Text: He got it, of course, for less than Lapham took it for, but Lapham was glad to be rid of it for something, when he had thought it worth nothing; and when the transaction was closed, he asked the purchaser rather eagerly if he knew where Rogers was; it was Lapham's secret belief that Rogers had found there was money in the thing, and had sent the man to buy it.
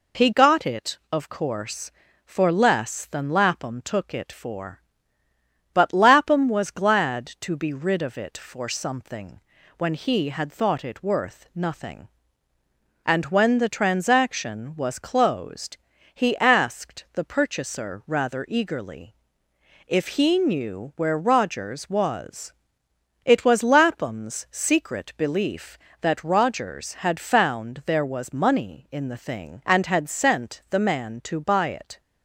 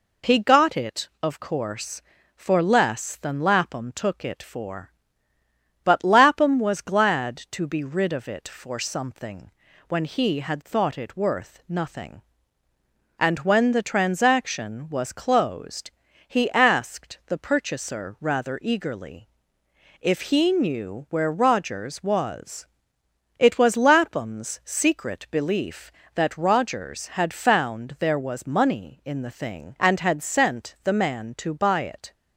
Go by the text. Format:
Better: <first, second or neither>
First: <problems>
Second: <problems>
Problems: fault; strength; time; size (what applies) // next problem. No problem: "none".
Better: neither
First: pauses between "eagerly" and "if"; noticeable; at 19.1 s; 0.72 s long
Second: pauses between "eagerly" and "if"; noticeable; at 19.2 s; 0.72 s long